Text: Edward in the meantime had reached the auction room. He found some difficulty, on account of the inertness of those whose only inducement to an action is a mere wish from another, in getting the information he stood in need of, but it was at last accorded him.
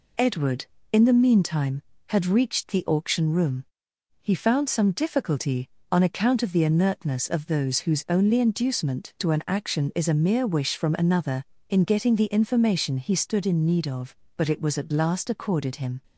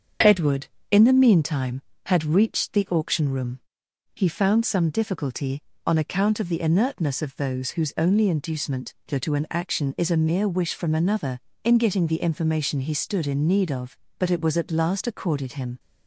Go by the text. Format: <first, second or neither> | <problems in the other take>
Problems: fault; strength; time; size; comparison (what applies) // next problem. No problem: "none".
first | starts louder than the rest; until 1.4 s; 7 dB // says "to" twice; at 9.1 s